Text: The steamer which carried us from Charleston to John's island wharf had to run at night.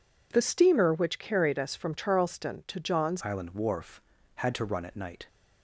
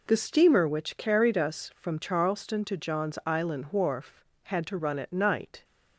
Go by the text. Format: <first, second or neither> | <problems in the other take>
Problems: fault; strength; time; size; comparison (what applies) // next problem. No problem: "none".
second | changes voice at "island"; from 3.2 s on; 2.0 s long